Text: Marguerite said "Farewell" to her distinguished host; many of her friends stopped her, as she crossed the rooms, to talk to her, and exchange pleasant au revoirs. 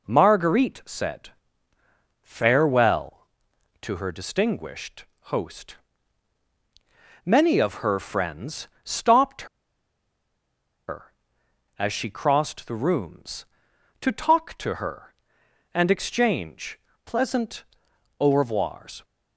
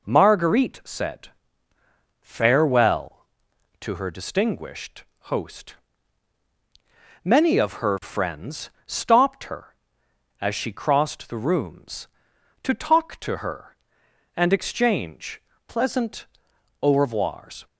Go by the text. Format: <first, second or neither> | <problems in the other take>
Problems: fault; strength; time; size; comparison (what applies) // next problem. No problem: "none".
second | pauses between "said" and "Farewell"; noticeable; at 1.2 s; 0.92 s long; noticeable in the second // pauses between "distinguished" and "host"; slight; at 5.0 s; 0.26 s long; slight in the second // pauses between "friends" and "stopped"; slight; at 8.6 s; 0.16 s long; slight in the second // pauses between "stopped" and "her"; strong; at 9.4 s; 1.4 s long // pauses between "exchange" and "pleasant"; slight; at 16.7 s; 0.24 s long; slight in the second // pauses between "pleasant" and "au"; noticeable; at 17.6 s; 0.54 s long; noticeable in the second